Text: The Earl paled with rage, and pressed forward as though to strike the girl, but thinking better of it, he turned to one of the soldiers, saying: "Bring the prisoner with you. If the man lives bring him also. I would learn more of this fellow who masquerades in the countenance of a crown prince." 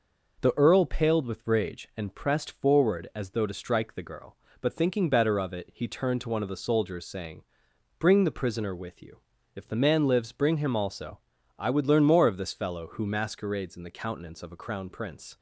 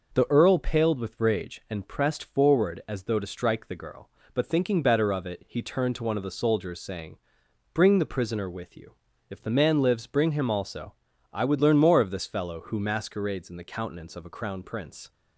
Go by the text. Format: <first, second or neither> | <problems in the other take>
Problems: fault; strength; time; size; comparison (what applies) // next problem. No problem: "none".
neither | none